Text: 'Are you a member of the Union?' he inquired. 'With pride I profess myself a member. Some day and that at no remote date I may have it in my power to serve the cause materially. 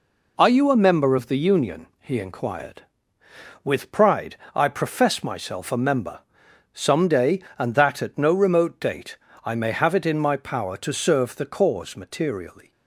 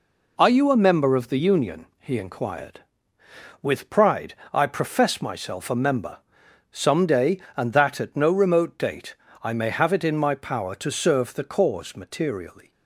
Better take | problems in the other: neither | pauses between "pride" and "I"; slight; the same in both // pauses between "date" and "I"; slight; the same in both

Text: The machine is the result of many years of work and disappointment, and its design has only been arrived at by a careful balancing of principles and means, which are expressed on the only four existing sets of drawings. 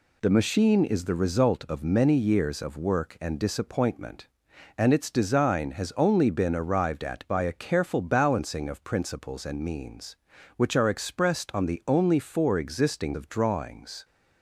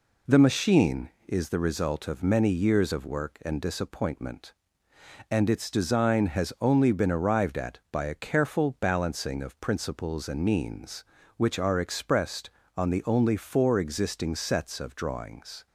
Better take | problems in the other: second | skips "sets"; at 13.1 s

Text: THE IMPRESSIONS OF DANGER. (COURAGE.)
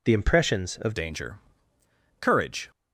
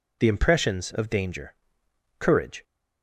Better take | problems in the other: second | changes voice at "DANGER"; from 0.9 s on; 1.8 s long

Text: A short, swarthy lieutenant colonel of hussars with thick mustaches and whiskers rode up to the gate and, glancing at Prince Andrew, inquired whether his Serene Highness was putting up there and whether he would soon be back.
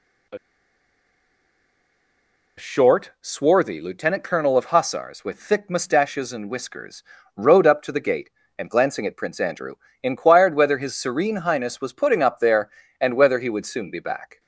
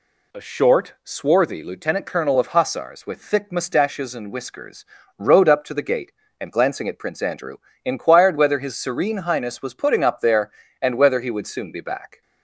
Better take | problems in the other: second | pauses between "A" and "short"; strong; at 0.3 s; 2.2 s long // pauses between "whiskers" and "rode"; slight; at 7.0 s; 0.32 s long; slight in the second

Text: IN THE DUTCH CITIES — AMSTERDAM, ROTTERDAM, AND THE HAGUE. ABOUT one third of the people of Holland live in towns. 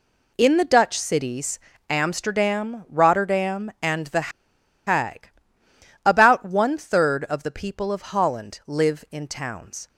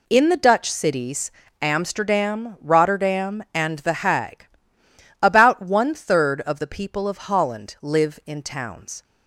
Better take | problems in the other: second | pauses between "THE" and "HAGUE"; noticeable; at 4.3 s; 0.56 s long

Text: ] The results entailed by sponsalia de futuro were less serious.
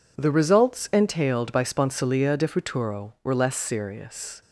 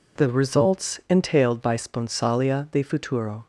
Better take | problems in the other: first | stops before "were less serious"; at 3.4 s

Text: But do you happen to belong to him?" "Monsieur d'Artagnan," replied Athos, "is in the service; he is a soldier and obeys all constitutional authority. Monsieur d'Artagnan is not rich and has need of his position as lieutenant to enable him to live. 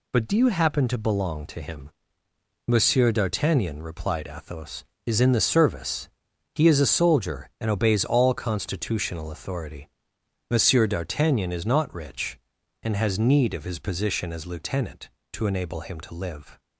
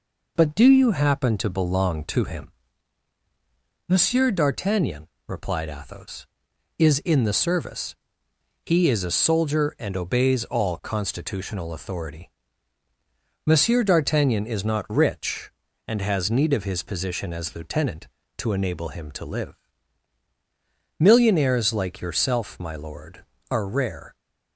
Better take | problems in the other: first | goes on to say "Millionaires like yourself my lord are rare"; strong; from 21.0 s on; 3.1 s long

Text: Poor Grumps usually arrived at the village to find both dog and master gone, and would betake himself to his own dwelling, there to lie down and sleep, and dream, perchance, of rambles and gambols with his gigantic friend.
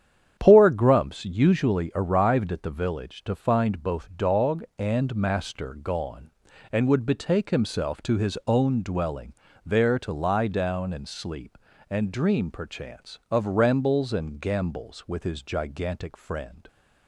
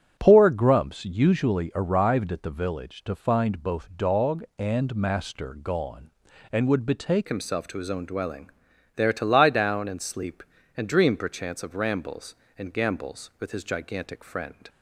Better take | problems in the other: first | starts louder than the rest; strong; until 1.1 s; 9 dB; strong in the first // changes voice at "himself"; from 7.2 s on; 7.4 s long

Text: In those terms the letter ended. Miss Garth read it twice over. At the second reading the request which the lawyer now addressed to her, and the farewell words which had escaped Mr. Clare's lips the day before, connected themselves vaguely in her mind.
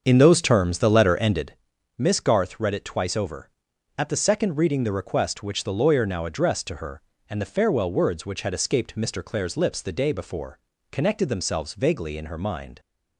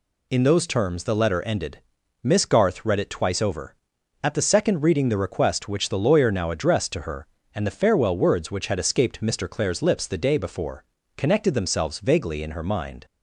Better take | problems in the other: second | starts louder than the rest; until 1.5 s; 7 dB

